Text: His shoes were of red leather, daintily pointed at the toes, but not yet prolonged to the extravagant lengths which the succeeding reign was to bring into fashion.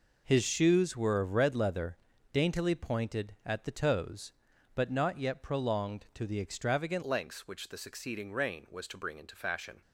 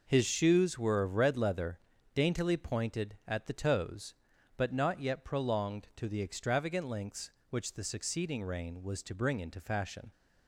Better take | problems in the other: second | changes voice at "lengths"; from 7.0 s on; 2.8 s long

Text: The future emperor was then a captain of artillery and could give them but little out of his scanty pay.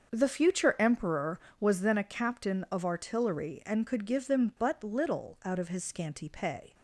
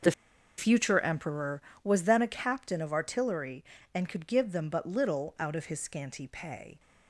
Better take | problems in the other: first | starts louder than the rest; noticeable; until 1.5 s; 6 dB; also in the first // pauses between "The" and "future"; noticeable; at 0.1 s; 0.46 s long

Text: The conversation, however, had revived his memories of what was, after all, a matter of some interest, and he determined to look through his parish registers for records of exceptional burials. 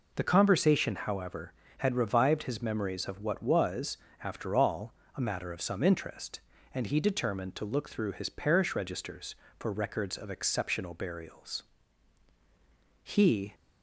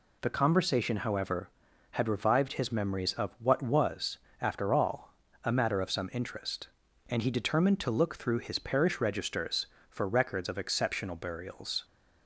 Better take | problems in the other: second | goes on to say "He"; from 13.0 s on; 0.52 s long

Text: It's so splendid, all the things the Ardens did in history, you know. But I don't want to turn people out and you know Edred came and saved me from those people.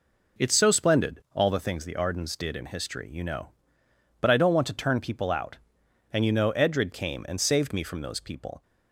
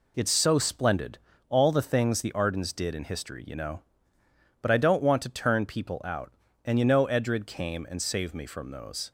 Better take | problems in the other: first | stops before "people"; at 9.0 s

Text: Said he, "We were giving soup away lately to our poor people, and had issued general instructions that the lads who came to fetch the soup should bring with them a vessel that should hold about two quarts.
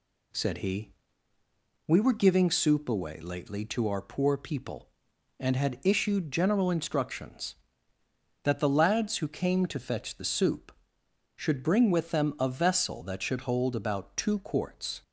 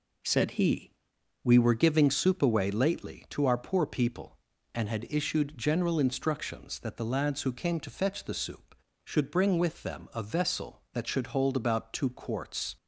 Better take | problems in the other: neither | none

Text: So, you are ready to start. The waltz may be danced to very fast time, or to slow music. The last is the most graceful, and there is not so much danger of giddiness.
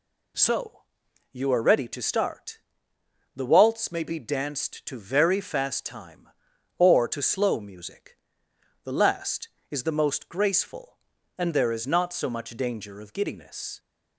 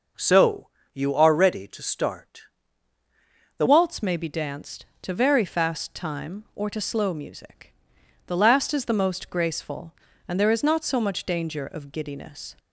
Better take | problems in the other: first | changes voice at "waltz"; from 3.6 s on; 8.9 s long

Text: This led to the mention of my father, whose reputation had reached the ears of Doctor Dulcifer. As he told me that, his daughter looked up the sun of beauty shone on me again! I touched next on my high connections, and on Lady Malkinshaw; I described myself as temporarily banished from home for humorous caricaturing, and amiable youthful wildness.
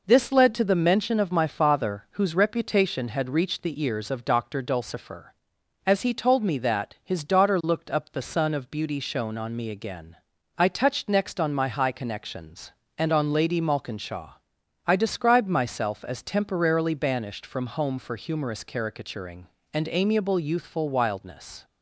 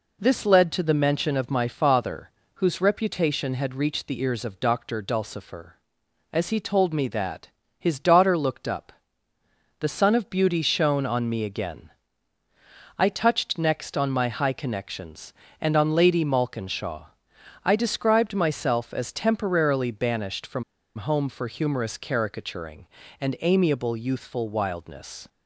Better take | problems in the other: first | pauses between "up" and "the"; noticeable; at 8.9 s; 0.88 s long // pauses between "from" and "home"; slight; at 20.6 s; 0.34 s long

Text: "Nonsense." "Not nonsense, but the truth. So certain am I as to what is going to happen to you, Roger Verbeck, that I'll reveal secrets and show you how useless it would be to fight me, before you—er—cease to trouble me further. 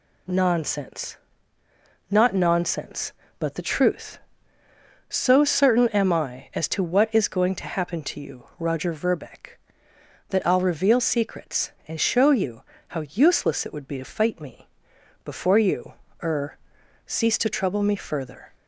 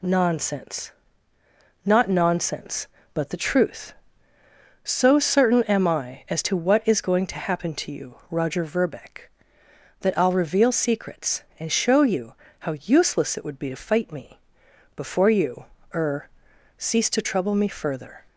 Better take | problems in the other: neither | pauses between "you" and "how"; slight; the same in both

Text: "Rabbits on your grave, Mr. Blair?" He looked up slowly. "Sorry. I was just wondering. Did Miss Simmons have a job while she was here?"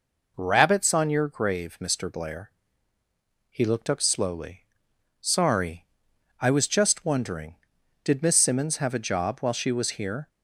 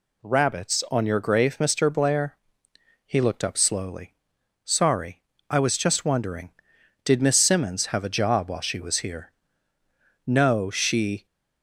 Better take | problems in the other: first | goes on to say "No she"; noticeable; from 10.2 s on; 0.98 s long

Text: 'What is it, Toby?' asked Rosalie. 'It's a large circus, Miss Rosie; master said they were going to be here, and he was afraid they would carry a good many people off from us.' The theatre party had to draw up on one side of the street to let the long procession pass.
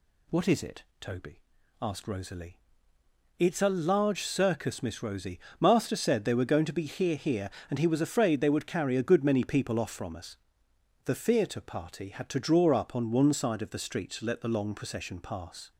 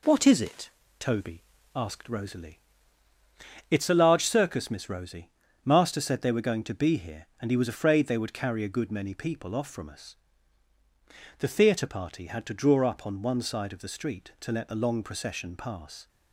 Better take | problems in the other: second | says "here" twice; at 7.1 s

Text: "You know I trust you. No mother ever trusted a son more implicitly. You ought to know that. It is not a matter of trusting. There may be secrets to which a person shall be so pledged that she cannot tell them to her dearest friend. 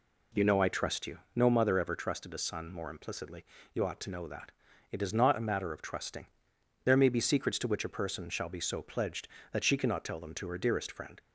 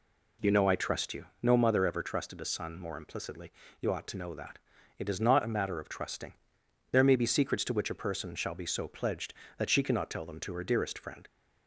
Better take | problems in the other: neither | none

